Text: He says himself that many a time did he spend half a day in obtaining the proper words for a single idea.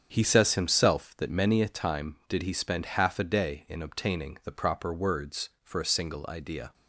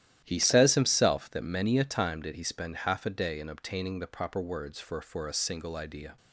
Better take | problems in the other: first | starts louder than the rest; strong; until 1.2 s; 12 dB; strong in the first // says "for" twice; at 5.0 s

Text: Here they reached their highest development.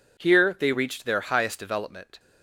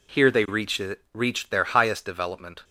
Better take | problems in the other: first | says "reached" twice; at 1.1 s

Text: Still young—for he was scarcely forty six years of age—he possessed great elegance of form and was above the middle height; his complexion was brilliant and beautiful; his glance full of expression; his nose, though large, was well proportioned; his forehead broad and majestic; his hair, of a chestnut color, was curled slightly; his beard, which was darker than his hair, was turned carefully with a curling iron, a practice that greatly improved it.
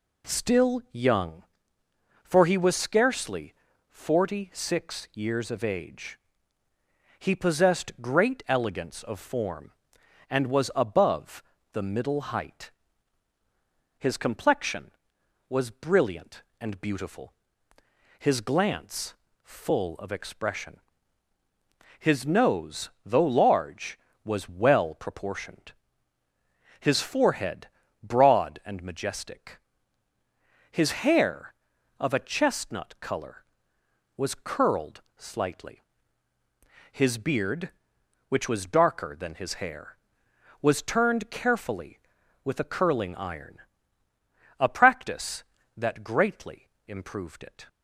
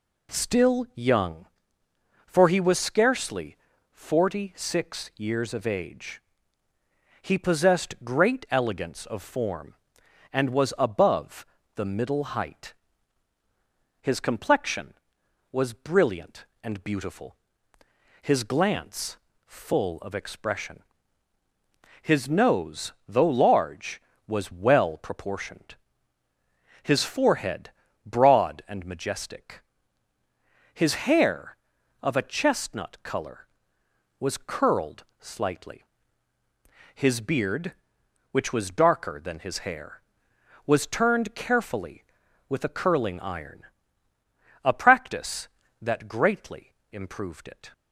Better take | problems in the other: neither | pauses between "scarcely" and "forty"; slight; the same in both // pauses between "above" and "the"; slight; the same in both // pauses between "glance" and "full"; slight; the same in both // pauses between "forehead" and "broad"; slight; the same in both // pauses between "curled" and "slightly"; slight; the same in both // pauses between "greatly" and "improved"; slight; the same in both

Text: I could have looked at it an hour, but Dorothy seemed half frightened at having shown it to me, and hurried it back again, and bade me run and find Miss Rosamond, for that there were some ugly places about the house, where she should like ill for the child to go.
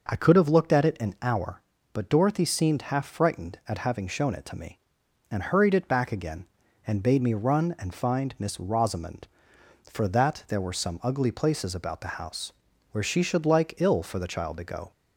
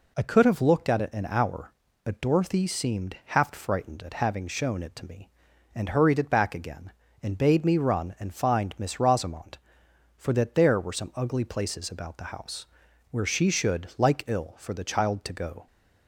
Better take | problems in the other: neither | none

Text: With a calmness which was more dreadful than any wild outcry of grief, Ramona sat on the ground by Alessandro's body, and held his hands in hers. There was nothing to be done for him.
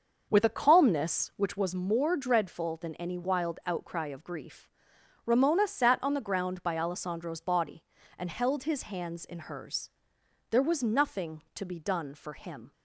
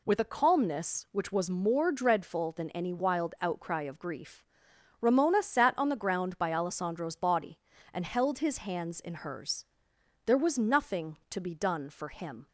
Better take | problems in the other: second | starts louder than the rest; until 1.5 s; 6.5 dB

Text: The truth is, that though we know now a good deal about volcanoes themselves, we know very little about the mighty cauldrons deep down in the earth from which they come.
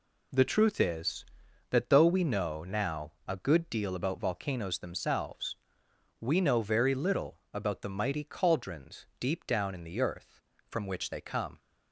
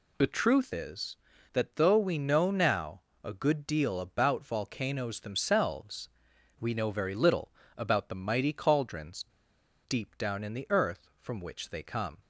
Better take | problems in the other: first | pauses between "now" and "a"; slight; at 3.0 s; 0.22 s long // pauses between "little" and "about"; slight; at 7.5 s; 0.24 s long; slight in the first // pauses between "cauldrons" and "deep"; noticeable; at 9.2 s; 0.63 s long

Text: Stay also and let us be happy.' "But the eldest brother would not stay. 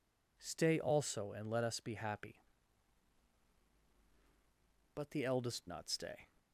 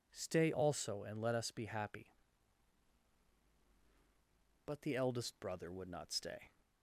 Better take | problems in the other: second | skips "brother would"; at 5.6 s

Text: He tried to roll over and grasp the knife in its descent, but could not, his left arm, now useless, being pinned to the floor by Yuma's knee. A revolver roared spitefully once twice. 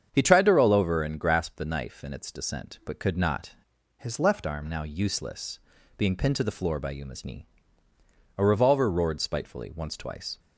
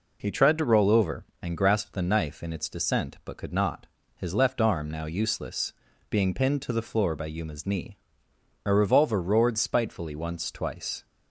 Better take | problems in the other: second | starts louder than the rest; strong; until 1.1 s; 7.5 dB // changes voice from "his" to "left"; from 3.9 to 4.4 s; 0.5 s long

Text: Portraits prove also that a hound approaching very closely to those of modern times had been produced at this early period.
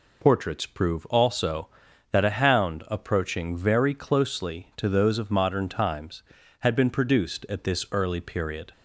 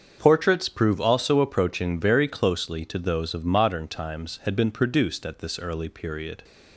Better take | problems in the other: first | starts louder than the rest; until 1.2 s; 7 dB // skips "that a hound"; at 1.3 s

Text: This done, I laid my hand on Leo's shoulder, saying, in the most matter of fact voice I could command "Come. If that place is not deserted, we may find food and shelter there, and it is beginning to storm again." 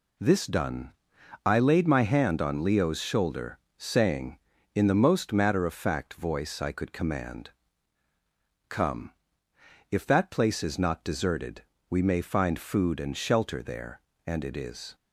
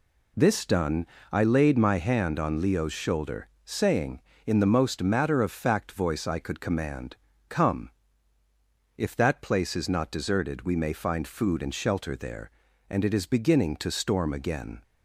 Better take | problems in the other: second | pauses between "command" and "Come"; at 7.5 s; 1.1 s long; slight in the second // stops before "beginning to storm again"; at 14.9 s

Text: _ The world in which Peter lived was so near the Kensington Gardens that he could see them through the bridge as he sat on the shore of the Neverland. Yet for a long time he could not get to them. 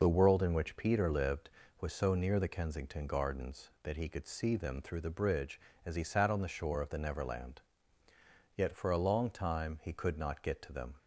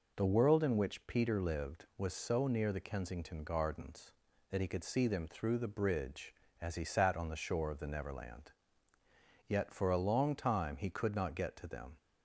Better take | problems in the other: neither | none

